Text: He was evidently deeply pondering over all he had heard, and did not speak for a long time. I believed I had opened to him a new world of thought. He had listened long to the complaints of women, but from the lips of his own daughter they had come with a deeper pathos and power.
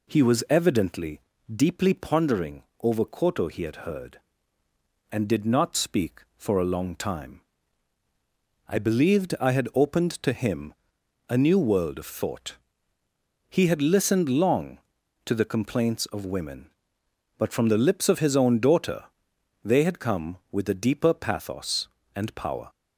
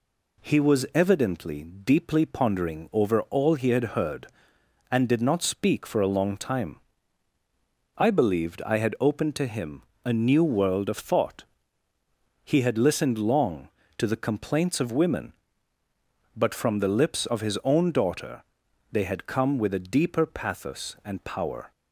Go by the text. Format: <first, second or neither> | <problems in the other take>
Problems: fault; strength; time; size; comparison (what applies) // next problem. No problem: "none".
second | pauses between "evidently" and "deeply"; slight; at 1.1 s; 0.34 s long // pauses between "pondering" and "over"; slight; at 2.6 s; 0.18 s long // says "koto" for "all"; at 3.0 s // pauses between "him" and "a"; noticeable; at 10.7 s; 0.54 s long; slight in the second // pauses between "daughter" and "they"; noticeable; at 19.0 s; 0.58 s long; noticeable in the second